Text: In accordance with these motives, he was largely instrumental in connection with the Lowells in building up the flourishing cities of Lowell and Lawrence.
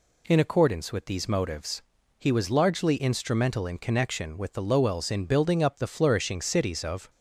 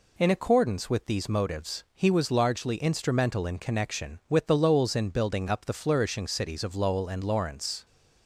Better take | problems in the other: second | stops before "Lowell and Lawrence"; at 7.0 s

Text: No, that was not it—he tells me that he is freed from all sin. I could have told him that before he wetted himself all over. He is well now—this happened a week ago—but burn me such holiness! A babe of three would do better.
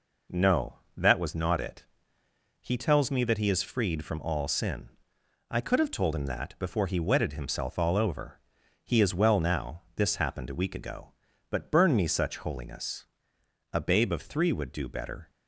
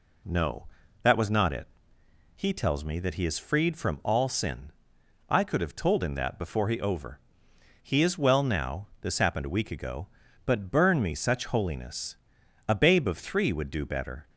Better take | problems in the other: first | skips "wetted himself all"; at 6.7 s

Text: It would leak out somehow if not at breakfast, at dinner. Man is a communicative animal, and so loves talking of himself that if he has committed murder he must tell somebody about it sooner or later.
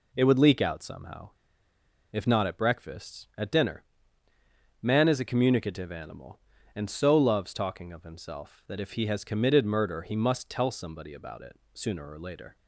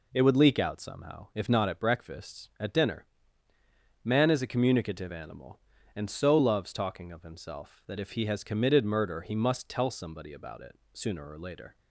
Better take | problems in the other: second | pauses between "somehow" and "if"; noticeable; at 1.2 s; 0.81 s long // pauses between "it" and "sooner"; slight; at 11.5 s; 0.18 s long; slight in the second

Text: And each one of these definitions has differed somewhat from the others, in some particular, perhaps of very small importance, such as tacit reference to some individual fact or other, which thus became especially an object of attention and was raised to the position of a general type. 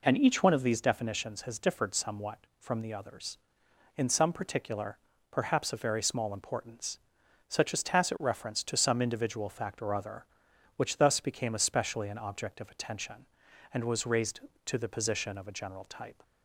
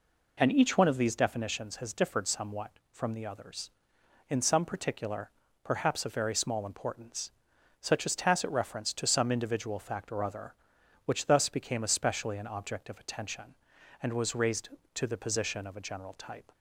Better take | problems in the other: neither | none

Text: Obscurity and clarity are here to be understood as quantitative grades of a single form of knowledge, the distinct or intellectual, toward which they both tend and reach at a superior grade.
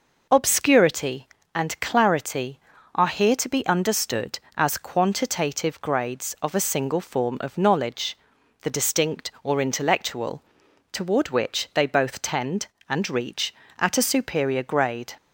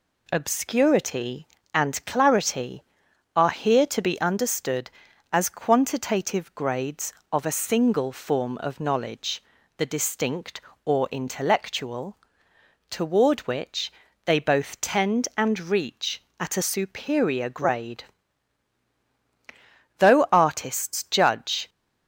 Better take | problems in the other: first | pauses between "which" and "they"; slight; at 13.9 s; 0.32 s long // goes on to say "Though artists judge"; strong; from 19.9 s on; 1.7 s long

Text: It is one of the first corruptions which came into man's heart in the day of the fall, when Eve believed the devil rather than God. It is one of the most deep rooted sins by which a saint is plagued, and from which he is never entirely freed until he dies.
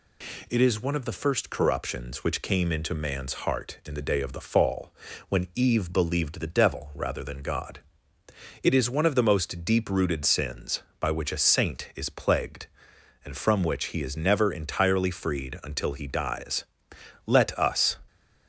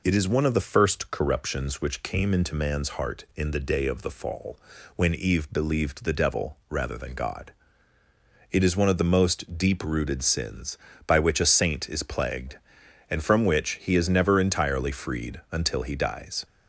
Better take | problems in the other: second | goes on to say "Let us"; noticeable; from 17.2 s on; 0.72 s long

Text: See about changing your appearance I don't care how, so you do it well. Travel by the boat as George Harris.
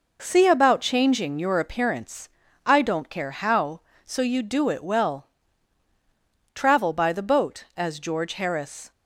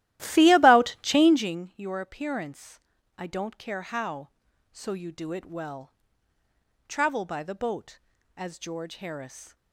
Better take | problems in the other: first | starts louder than the rest; strong; until 1.6 s; 14.5 dB // pauses between "appearance" and "I"; at 2.7 s; 0.38 s long; also in the first

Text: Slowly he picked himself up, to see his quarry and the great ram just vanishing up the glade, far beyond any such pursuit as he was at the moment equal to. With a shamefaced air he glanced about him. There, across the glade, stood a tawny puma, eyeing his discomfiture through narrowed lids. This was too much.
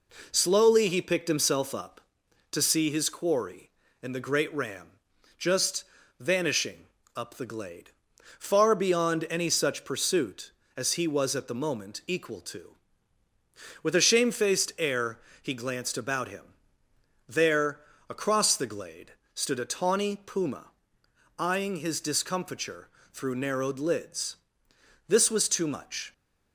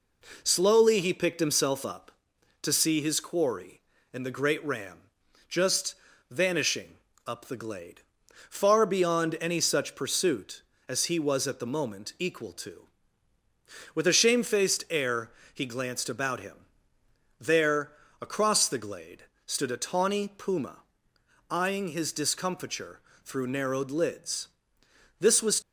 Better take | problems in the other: first | pauses between "ram" and "just"; noticeable; at 4.9 s; 0.50 s long; noticeable in the first // pauses between "just" and "vanishing"; slight; at 5.9 s; 0.34 s long; slight in the first // pauses between "vanishing" and "up"; slight; at 6.9 s; 0.30 s long; slight in the first // pauses between "air" and "he"; slight; at 15.3 s; 0.24 s long; slight in the first // pauses between "discomfiture" and "through"; slight; at 23.0 s; 0.24 s long; slight in the first // stops before "too much"; at 25.6 s

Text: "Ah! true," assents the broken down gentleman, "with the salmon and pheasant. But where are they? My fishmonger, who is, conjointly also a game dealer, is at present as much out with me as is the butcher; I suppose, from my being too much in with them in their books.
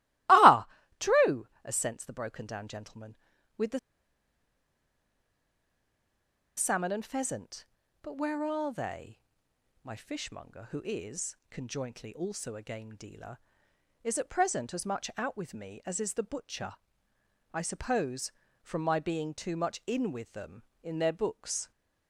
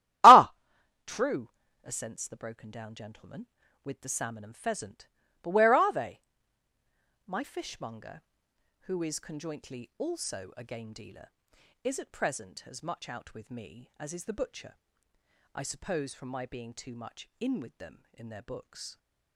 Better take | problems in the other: second | starts louder than the rest; strong; until 1.8 s; 18.5 dB; strong in the second // pauses between "the" and "salmon"; strong; at 3.7 s; 2.7 s long

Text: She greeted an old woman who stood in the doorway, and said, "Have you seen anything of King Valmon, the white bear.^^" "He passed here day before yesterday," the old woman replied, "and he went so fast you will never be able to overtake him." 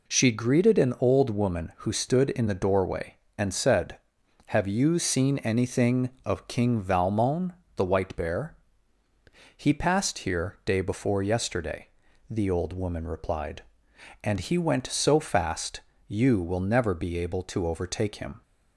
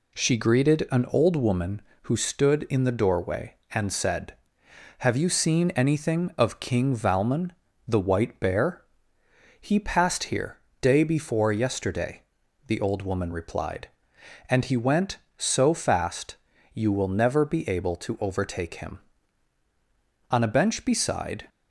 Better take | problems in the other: first | pauses between "here" and "day"; slight; at 10.5 s; 0.24 s long // pauses between "fast" and "you"; at 16.3 s; 0.38 s long; slight in the first // goes on to say "On a bench beside"; noticeable; from 20.3 s on; 1.1 s long

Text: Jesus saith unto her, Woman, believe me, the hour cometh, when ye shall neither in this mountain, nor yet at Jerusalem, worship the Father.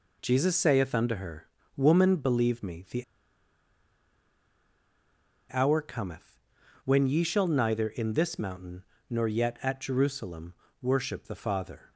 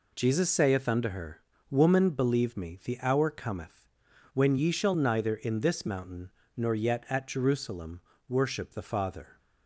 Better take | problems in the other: second | pauses between "the" and "hour"; strong; at 3.0 s; 2.4 s long

